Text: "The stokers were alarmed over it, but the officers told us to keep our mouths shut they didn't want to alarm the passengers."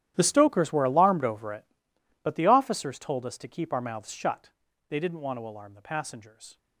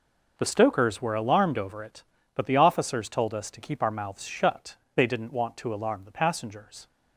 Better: second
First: gets quieter; strong; throughout; 19 dB // pauses between "shut" and "they"; at 4.4 s; 0.38 s long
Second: pauses between "shut" and "they"; slight; at 4.7 s; 0.20 s long

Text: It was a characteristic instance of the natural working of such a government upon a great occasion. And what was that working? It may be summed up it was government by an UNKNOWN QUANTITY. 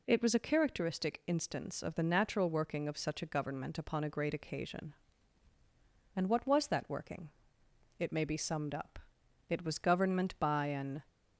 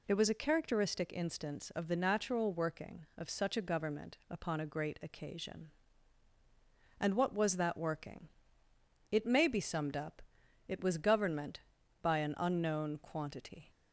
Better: second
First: pauses between "up" and "it"; noticeable; at 8.9 s; 0.48 s long // stops before "UNKNOWN QUANTITY"; at 11.0 s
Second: pauses between "up" and "it"; noticeable; at 10.1 s; 0.46 s long

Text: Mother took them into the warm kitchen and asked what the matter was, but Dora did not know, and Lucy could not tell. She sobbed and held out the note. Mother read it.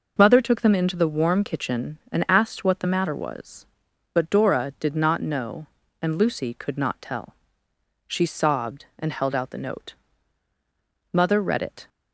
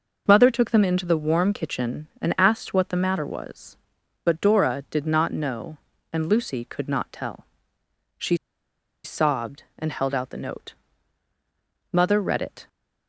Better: first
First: none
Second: pauses between "She" and "sobbed"; noticeable; at 8.3 s; 0.69 s long

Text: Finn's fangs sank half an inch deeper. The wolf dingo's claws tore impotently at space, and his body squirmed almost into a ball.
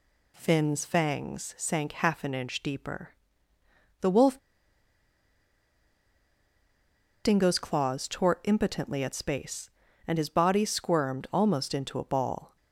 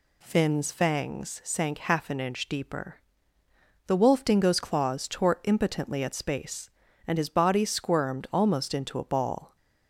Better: second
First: pauses between "wolf" and "dingo's"; strong; at 4.3 s; 2.8 s long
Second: none

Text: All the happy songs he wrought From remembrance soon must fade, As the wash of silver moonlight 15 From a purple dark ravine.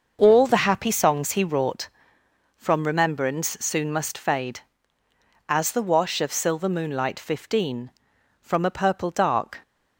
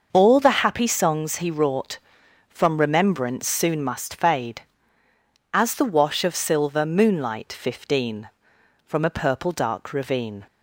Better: second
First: starts louder than the rest; noticeable; until 1.2 s; 6 dB // stops before "ravine"; at 9.6 s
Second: starts louder than the rest; noticeable; until 1.1 s; 6 dB

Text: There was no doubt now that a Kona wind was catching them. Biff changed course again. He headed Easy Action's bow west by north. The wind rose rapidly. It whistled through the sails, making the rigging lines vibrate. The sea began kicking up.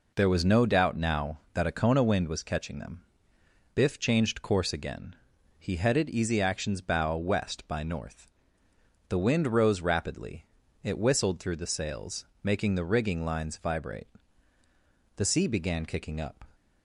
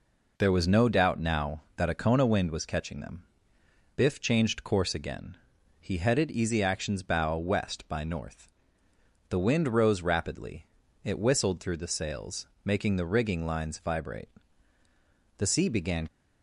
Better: first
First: none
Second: stops before "kicking up"; at 16.0 s

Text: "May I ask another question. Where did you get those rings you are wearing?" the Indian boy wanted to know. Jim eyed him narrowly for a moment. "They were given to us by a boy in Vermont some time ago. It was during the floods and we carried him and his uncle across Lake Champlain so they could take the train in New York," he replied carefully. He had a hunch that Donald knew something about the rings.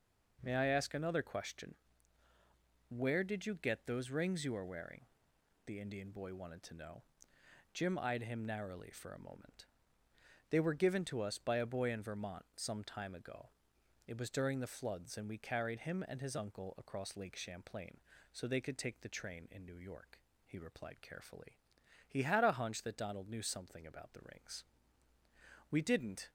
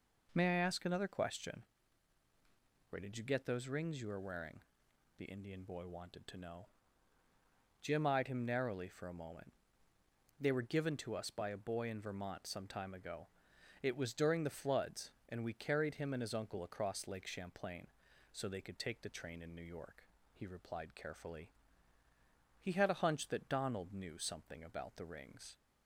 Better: second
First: goes on to say "We didn't"; from 25.6 s on; 0.60 s long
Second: none

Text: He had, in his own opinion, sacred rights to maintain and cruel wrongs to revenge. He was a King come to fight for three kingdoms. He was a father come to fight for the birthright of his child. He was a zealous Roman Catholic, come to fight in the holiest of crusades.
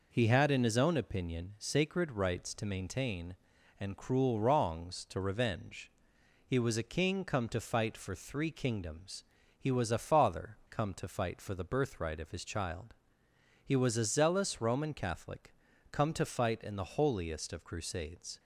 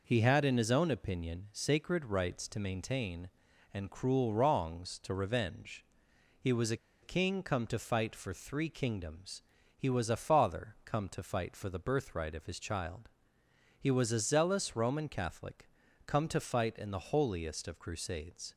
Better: first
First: none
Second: pauses between "a" and "King"; slight; at 6.7 s; 0.27 s long

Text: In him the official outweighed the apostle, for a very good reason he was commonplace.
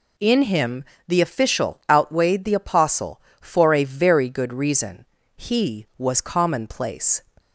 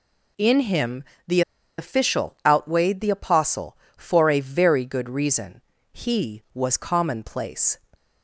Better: first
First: pauses between "him" and "the"; slight; at 0.8 s; 0.24 s long // pauses between "reason" and "he"; slight; at 5.0 s; 0.32 s long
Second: pauses between "him" and "the"; slight; at 1.0 s; 0.24 s long // pauses between "the" and "official"; at 1.4 s; 0.37 s long // pauses between "reason" and "he"; slight; at 5.6 s; 0.32 s long

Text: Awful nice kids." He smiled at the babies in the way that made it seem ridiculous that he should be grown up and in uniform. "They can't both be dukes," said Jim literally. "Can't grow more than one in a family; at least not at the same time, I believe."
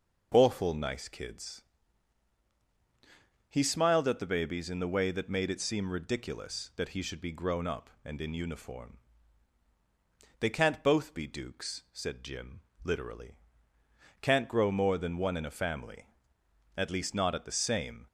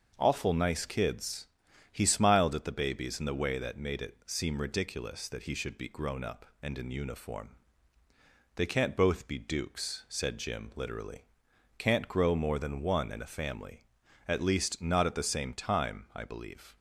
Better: second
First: pauses between "Jim" and "literally"; slight; at 12.6 s; 0.20 s long // stops before "time I believe"; at 18.0 s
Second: none

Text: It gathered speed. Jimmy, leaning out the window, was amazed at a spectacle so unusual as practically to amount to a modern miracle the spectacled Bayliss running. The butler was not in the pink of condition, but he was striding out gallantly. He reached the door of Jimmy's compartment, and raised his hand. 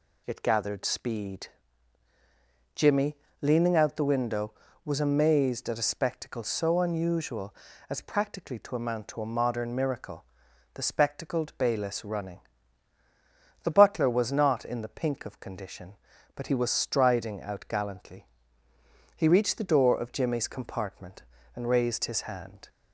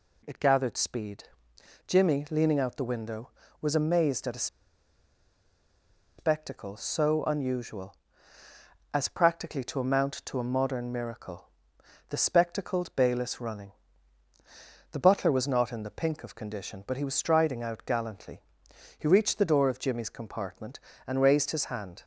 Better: first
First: pauses between "miracle" and "the"; noticeable; at 10.2 s; 0.50 s long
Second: pauses between "a" and "spectacle"; strong; at 4.4 s; 1.7 s long // pauses between "miracle" and "the"; noticeable; at 11.4 s; 0.60 s long

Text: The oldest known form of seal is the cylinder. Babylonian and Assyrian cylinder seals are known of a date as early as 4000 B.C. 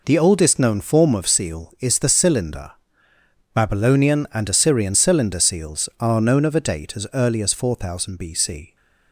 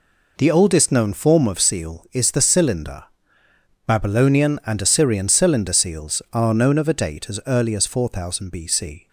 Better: neither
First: none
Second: none

